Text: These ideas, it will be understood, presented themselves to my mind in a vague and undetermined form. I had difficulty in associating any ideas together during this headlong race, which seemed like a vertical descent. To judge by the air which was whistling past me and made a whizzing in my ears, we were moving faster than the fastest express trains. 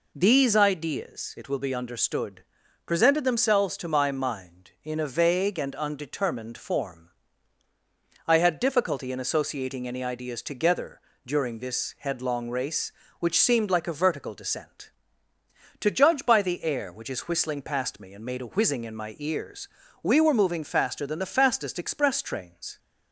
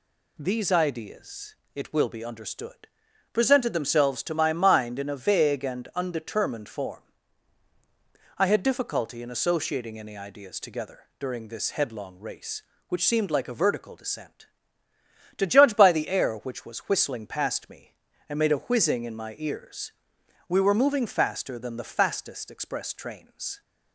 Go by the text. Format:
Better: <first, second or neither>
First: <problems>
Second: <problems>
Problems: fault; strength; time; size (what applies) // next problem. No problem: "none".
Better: second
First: pauses between "together" and "during"; slight; at 11.0 s; 0.26 s long // says "is" for "was"; at 17.1 s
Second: pauses between "together" and "during"; slight; at 11.0 s; 0.18 s long